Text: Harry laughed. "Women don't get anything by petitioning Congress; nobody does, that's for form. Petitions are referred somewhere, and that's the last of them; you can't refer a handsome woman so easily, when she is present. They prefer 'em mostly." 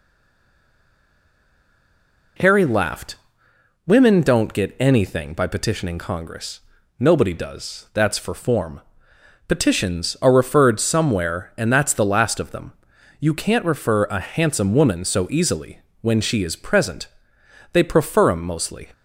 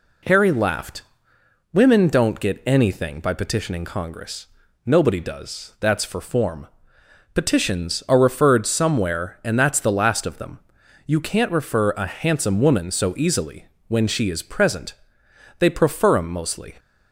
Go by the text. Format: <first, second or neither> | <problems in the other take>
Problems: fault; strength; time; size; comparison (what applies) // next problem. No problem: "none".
second | stays silent before the first word; until 2.3 s; 2.3 s long